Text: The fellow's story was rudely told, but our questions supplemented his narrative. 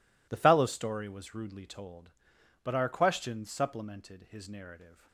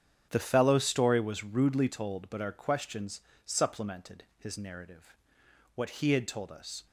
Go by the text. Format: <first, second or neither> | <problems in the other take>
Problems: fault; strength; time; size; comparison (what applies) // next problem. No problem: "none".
first | starts louder than the rest; strong; until 1.3 s; 8.5 dB // pauses between "questions" and "supplemented"; slight; at 3.2 s; 0.24 s long // goes on to say "What he had told us"; noticeable; from 5.7 s on; 1.1 s long